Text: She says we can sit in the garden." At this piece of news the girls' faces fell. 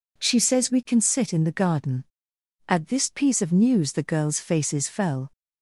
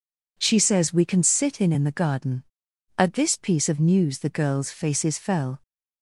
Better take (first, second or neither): first